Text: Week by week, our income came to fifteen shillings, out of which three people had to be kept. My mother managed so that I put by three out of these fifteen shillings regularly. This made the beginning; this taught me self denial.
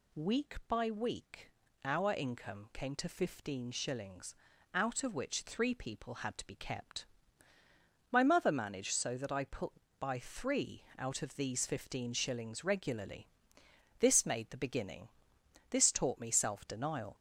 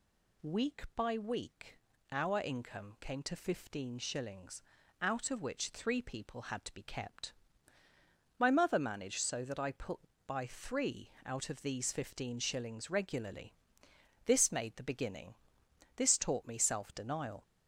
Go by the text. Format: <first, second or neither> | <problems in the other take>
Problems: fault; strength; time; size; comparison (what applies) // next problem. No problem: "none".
neither | pauses between "three" and "out"; slight; the same in both